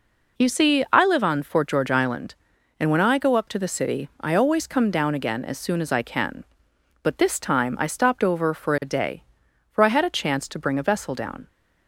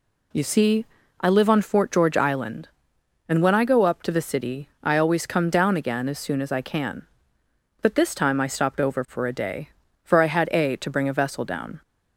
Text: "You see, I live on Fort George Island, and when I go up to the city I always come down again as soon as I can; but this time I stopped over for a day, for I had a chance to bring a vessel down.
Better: first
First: none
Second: skips "chance"; at 10.7 s

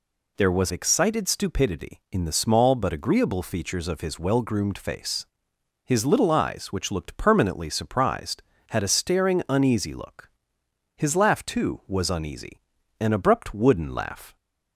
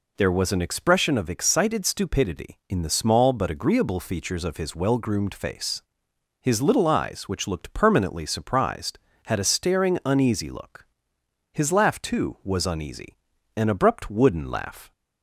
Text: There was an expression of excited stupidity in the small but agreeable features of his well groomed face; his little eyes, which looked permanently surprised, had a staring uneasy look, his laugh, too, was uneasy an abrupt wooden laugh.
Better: second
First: skips "an expression of"; at 0.7 s // pauses between "uneasy" and "an"; at 12.5 s; 0.40 s long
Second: pauses between "uneasy" and "an"; at 13.1 s; 0.40 s long

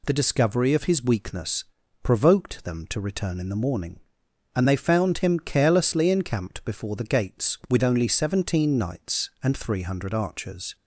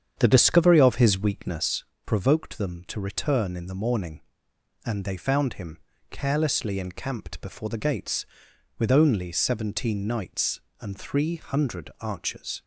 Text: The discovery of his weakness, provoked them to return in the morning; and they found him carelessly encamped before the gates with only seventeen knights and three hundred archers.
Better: first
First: none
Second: starts louder than the rest; strong; until 1.9 s; 8 dB // pauses between "him" and "carelessly"; slight; at 5.7 s; 0.32 s long

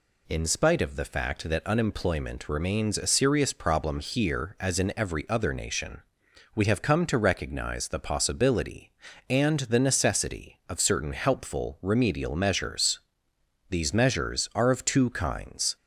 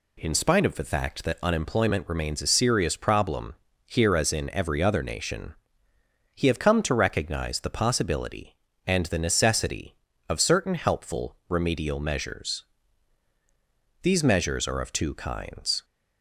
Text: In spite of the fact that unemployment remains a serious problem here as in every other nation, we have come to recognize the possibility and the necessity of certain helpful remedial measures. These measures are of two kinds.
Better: first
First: none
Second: pauses between "problem" and "here"; slight; at 3.5 s; 0.30 s long // says "he" for "we"; at 6.3 s

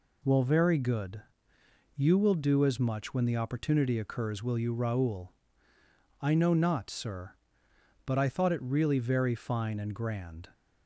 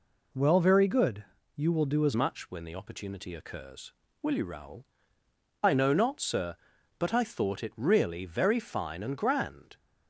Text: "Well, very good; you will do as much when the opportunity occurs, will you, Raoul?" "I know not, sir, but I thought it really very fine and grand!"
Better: first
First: none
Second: changes voice at "much"; from 2.1 s on; 7.6 s long

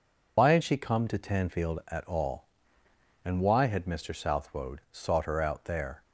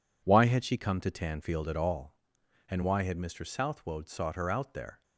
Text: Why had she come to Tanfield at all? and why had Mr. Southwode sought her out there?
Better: second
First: loses the start of "Why"; at 0.3 s; 55 ms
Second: none

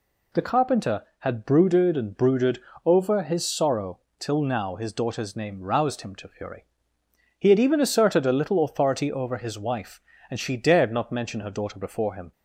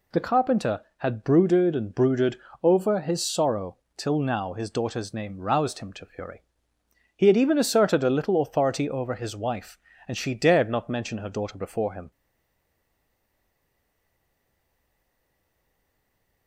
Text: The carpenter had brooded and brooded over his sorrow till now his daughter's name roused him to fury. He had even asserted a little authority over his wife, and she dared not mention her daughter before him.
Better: first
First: pauses between "brooded" and "over"; slight; at 2.5 s; 0.26 s long // pauses between "sorrow" and "till"; slight; at 3.9 s; 0.20 s long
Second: pauses between "brooded" and "over"; slight; at 2.3 s; 0.26 s long // pauses between "sorrow" and "till"; slight; at 3.7 s; 0.20 s long // stays silent after the last word; strong; from 12.1 s on; 4.3 s long

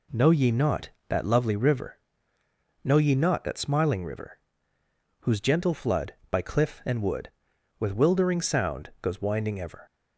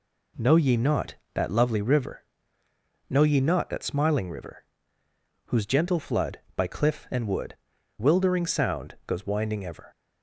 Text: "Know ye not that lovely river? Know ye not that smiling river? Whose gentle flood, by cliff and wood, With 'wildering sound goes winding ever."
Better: first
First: none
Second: skips "With"; at 7.7 s

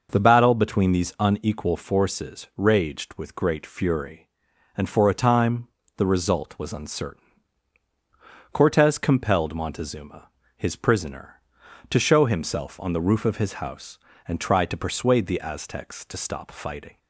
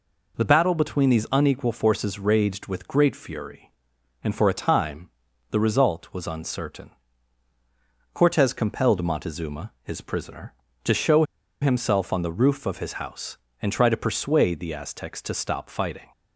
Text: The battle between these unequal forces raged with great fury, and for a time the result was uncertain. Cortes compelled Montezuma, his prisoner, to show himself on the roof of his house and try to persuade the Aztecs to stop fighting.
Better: first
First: pauses between "time" and "the"; slight; at 5.6 s; 0.30 s long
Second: pauses between "time" and "the"; at 5.0 s; 0.40 s long // pauses between "show" and "himself"; at 11.2 s; 0.38 s long

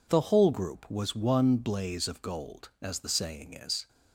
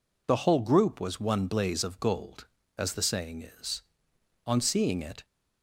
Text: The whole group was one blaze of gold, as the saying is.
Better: first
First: none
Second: goes on to say "On seeing it"; noticeable; from 4.4 s on; 0.78 s long

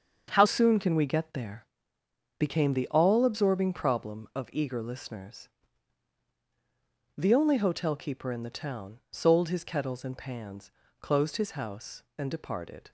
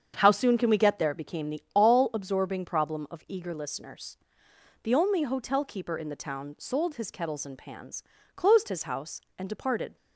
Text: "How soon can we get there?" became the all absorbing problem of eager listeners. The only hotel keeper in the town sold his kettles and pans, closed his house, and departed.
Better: second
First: starts louder than the rest; until 1.3 s; 7 dB // changes voice at "soon"; from 0.4 s on; 12.5 s long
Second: starts louder than the rest; strong; until 1.1 s; 7.5 dB

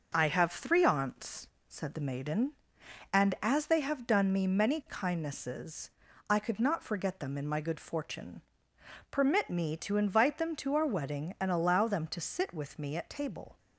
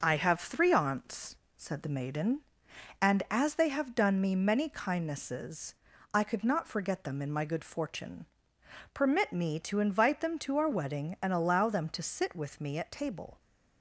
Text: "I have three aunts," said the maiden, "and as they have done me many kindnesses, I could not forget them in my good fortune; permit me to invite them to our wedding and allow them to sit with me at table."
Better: neither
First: none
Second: none

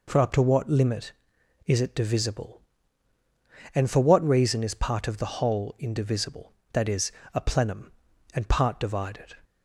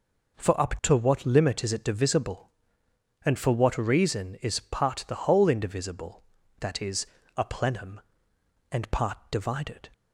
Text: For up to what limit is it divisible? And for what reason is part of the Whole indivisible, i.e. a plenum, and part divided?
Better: first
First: none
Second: skips "of"; at 5.0 s

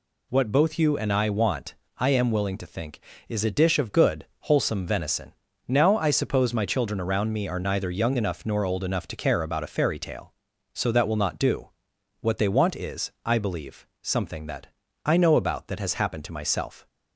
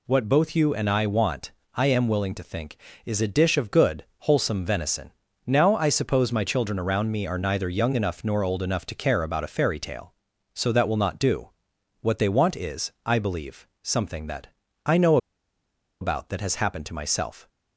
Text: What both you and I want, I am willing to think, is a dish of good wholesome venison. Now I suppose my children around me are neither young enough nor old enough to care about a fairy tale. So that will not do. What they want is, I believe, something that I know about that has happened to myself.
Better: first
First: pauses between "that" and "I"; at 14.6 s; 0.38 s long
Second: pauses between "that" and "I"; at 14.4 s; 0.38 s long // pauses between "know" and "about"; noticeable; at 15.1 s; 0.84 s long

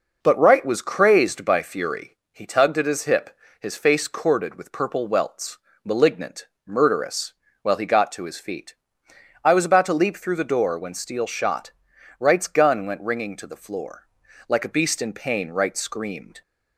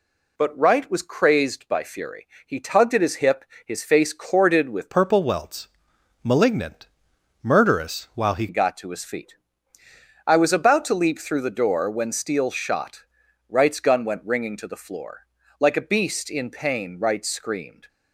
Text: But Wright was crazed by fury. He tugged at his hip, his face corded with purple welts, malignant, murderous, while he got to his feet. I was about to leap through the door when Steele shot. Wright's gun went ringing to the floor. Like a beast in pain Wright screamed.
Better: first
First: none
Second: changes voice from "purple" to "he"; from 4.9 to 8.4 s; 3.5 s long

